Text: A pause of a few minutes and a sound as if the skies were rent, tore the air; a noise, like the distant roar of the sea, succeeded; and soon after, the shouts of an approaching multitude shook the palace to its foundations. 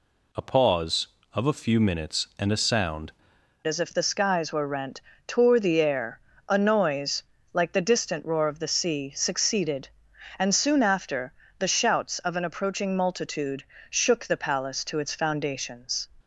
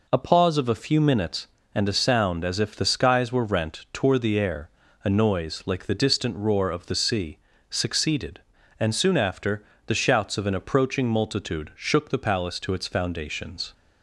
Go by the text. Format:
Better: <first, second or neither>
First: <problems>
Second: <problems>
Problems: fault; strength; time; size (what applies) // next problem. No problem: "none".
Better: second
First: changes voice at "as"; from 3.6 s on; 12.4 s long // pauses between "multitude" and "shook"; slight; at 13.6 s; 0.26 s long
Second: none